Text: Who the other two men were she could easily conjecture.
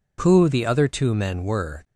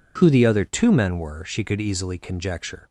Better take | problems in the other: second | stops before "she could easily conjecture"; at 1.8 s

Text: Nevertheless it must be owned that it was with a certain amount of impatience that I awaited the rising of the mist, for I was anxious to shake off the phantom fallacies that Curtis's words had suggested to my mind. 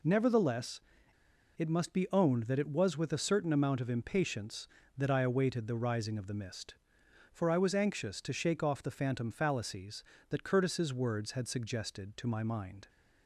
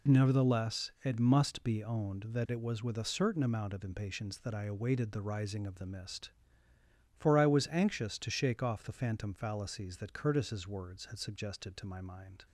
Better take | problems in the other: second | pauses between "Nevertheless" and "it"; noticeable; at 0.7 s; 0.78 s long

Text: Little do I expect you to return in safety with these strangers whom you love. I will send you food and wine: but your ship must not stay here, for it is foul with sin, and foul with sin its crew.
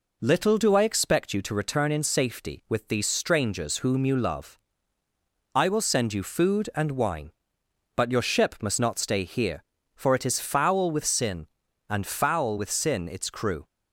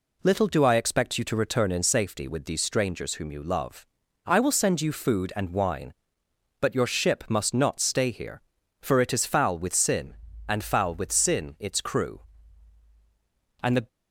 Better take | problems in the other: first | goes on to say "And the"; slight; from 13.6 s on; 0.26 s long

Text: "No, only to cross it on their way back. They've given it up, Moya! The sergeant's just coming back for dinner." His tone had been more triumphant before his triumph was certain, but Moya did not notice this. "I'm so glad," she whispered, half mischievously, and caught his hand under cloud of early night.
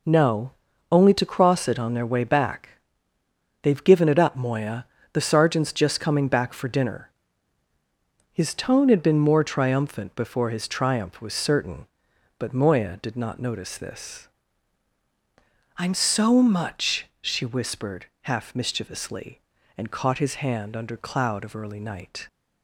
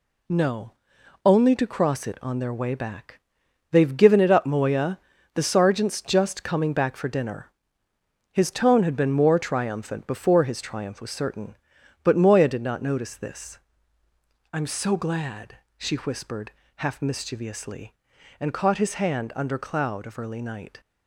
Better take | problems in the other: second | says "much" for "glad"; at 16.4 s

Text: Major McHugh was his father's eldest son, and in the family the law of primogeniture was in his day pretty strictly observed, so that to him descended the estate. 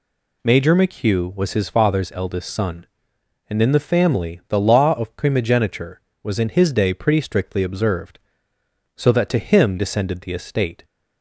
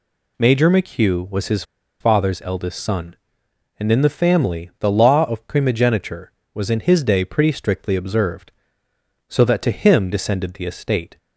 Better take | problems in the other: first | pauses between "his" and "father's"; at 1.6 s; 0.37 s long

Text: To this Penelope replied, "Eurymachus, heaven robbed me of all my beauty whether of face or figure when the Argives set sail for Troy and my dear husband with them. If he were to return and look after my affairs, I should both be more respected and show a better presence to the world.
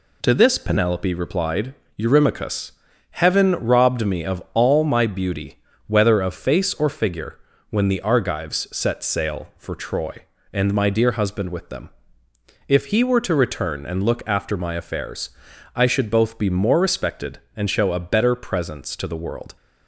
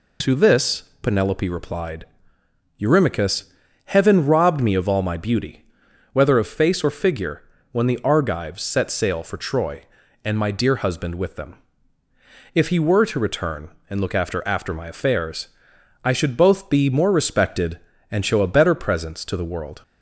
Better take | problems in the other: first | pauses between "this" and "Penelope"; slight; at 0.8 s; 0.18 s long // pauses between "beauty" and "whether"; noticeable; at 5.6 s; 0.48 s long; slight in the first // pauses between "figure" and "when"; slight; at 7.4 s; 0.30 s long; slight in the first // says "after" twice; at 14.4 s

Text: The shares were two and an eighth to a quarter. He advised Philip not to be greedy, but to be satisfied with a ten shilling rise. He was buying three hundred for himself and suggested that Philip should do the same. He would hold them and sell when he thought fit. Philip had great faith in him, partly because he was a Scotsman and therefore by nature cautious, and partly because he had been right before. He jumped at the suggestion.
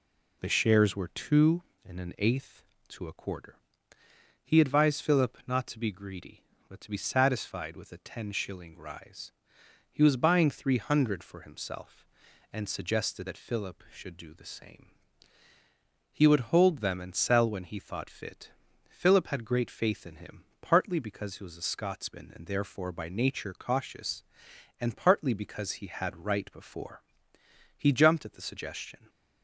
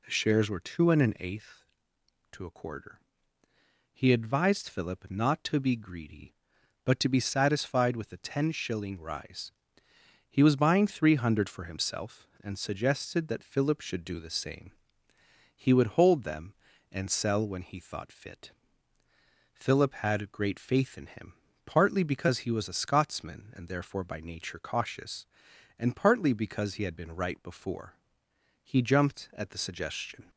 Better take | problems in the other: second | skips "been"; at 26.2 s

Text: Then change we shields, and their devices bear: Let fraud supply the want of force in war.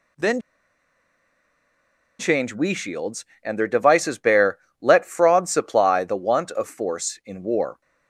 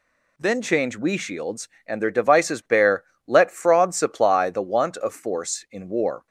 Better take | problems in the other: second | pauses between "Then" and "change"; strong; at 0.4 s; 1.7 s long

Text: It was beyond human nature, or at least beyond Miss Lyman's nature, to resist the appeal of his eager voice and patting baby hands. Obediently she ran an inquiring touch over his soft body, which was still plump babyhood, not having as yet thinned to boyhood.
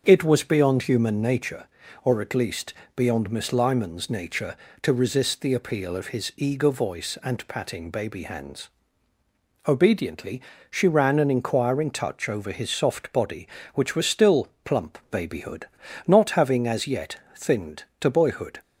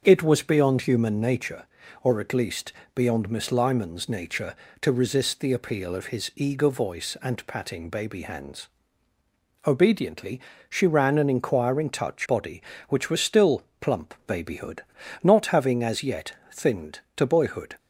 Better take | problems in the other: first | starts louder than the rest; until 1.0 s; 6.5 dB; also in the first // pauses between "least" and "beyond"; slight; at 2.7 s; 0.20 s long; slight in the first // pauses between "Obediently" and "she"; slight; at 10.4 s; 0.26 s long; slight in the first // skips "over his soft"; at 12.2 s // pauses between "still" and "plump"; slight; at 13.6 s; 0.20 s long; slight in the first // pauses between "yet" and "thinned"; slight; at 16.3 s; 0.22 s long; slight in the first

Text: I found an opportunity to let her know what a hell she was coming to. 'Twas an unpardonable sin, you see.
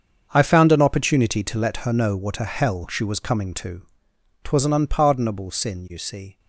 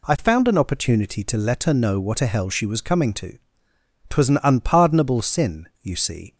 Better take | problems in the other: second | gets quieter; strong; throughout; 14.5 dB

